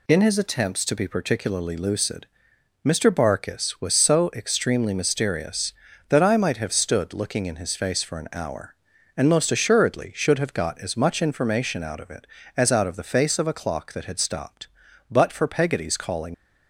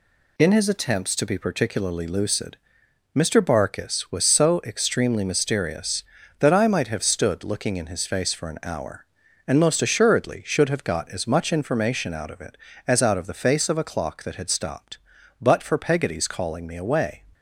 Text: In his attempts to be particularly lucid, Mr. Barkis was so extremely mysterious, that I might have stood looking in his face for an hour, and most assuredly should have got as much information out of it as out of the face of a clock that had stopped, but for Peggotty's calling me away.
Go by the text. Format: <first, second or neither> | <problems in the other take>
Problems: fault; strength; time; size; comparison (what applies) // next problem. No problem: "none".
second | stops before "me away"; at 16.3 s